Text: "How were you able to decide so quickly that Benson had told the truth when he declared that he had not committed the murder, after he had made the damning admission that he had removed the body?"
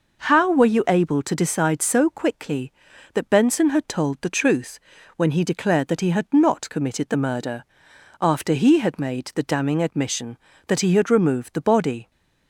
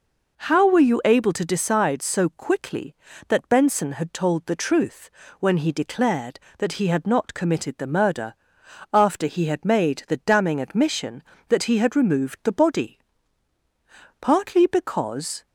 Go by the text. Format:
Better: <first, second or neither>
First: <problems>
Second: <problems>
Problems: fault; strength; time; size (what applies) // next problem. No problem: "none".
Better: first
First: pauses between "truth" and "when"; at 4.7 s; 0.38 s long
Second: pauses between "truth" and "when"; slight; at 5.0 s; 0.30 s long // goes on to say "Partly because"; noticeable; from 14.1 s on; 1.2 s long